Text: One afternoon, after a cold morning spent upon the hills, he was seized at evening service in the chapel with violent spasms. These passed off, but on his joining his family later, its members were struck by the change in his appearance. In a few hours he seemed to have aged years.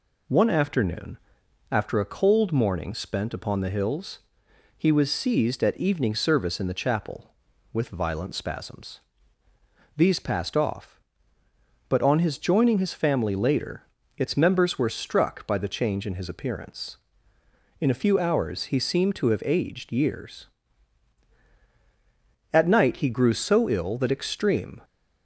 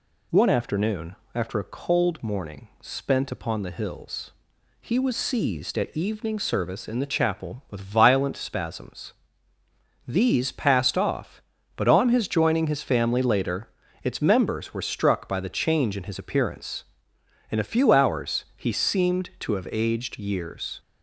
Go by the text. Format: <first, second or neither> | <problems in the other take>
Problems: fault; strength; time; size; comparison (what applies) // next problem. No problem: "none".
second | goes on to say "At night he grew so ill that extreme"; strong; from 22.5 s on; 2.3 s long